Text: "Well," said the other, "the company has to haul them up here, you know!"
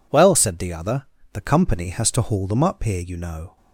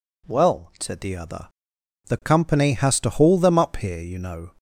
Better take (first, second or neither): neither